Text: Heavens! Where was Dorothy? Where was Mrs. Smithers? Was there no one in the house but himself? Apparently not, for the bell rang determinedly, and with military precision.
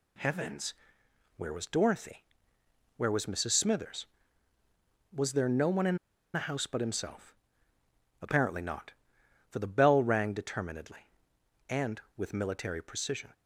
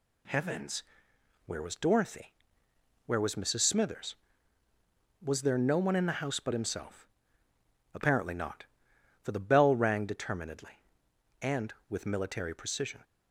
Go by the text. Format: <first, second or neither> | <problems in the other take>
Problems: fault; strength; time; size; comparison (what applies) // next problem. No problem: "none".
second | pauses between "in" and "the"; at 5.9 s; 0.37 s long